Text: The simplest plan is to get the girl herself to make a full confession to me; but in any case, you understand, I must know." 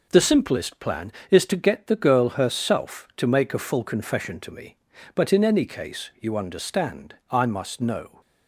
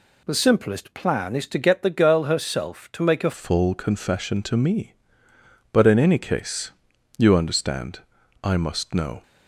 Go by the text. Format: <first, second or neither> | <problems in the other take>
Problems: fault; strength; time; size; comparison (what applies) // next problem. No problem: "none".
first | changes voice at "full"; from 3.3 s on; 5.9 s long